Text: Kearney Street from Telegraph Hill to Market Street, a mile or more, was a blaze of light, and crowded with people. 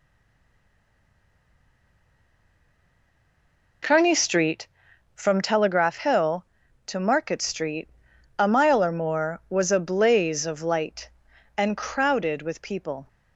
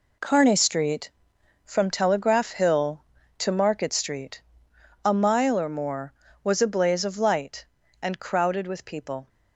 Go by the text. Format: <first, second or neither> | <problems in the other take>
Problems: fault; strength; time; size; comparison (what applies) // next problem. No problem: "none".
second | stays silent before the first word; strong; until 3.8 s; 3.8 s long